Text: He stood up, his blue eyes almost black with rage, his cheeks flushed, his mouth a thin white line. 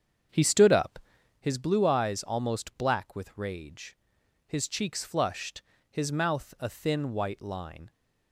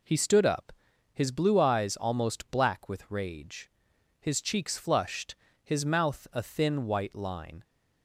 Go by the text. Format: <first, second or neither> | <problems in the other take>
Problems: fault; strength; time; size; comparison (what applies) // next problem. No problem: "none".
second | starts louder than the rest; strong; until 1.4 s; 7.5 dB